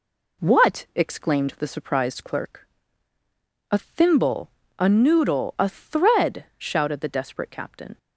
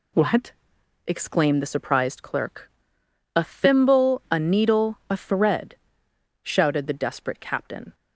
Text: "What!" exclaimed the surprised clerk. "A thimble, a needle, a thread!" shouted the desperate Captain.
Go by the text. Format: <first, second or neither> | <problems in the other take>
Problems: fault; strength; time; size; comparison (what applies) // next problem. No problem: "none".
second | says "noodle" for "needle"; at 4.8 s